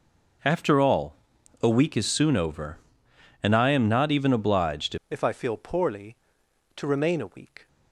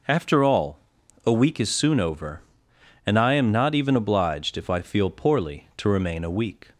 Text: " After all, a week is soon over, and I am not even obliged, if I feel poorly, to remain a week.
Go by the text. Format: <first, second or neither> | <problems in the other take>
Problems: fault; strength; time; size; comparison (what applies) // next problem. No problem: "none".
second | changes voice at "if"; from 5.0 s on; 2.6 s long